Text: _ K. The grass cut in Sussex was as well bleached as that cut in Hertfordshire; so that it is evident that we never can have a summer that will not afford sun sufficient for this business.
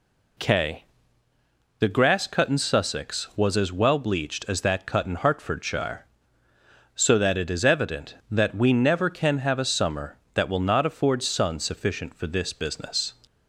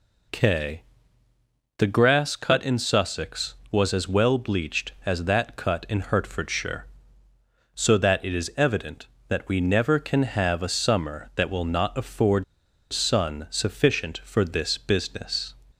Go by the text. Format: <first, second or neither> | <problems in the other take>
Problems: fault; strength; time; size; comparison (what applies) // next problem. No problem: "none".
first | pauses between "afford" and "sun"; noticeable; at 12.4 s; 0.47 s long